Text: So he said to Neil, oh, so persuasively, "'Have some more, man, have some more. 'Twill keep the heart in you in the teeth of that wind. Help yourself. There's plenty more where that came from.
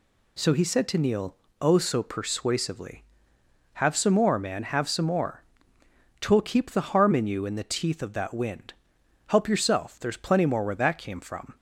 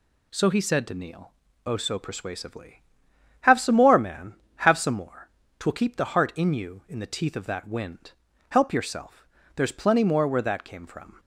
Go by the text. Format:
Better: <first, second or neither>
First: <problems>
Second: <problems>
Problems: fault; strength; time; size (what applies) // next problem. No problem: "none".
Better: second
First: says "harm" for "heart"; at 6.9 s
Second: none